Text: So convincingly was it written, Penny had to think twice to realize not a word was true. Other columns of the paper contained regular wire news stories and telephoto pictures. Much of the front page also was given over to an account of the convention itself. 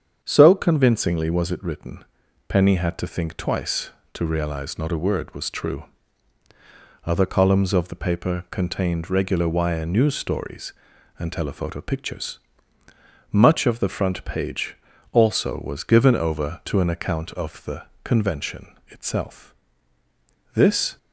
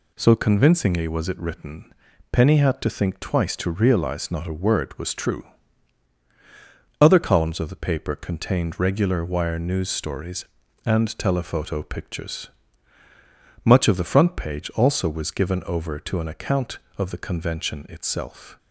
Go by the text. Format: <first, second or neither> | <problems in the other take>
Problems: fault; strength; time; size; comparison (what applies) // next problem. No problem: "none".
second | starts louder than the rest; strong; until 1.2 s; 7.5 dB // pauses between "page" and "also"; slight; at 14.7 s; 0.36 s long // pauses between "the" and "convention"; slight; at 17.8 s; 0.18 s long // goes on to say "This"; slight; from 20.5 s on; 0.44 s long